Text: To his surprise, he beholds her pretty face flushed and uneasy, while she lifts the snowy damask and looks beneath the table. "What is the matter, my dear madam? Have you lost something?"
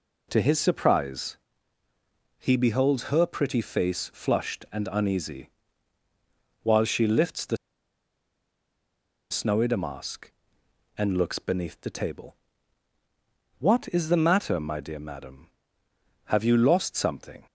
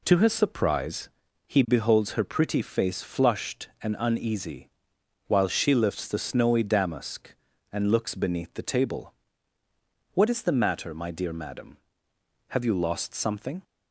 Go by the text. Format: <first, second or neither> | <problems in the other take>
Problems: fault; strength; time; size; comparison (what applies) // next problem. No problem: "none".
second | pauses between "the" and "snowy"; strong; at 7.5 s; 1.7 s long